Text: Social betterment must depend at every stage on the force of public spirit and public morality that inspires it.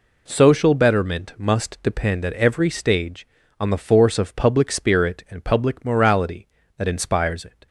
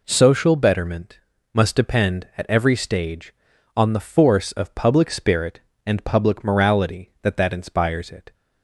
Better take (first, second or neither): first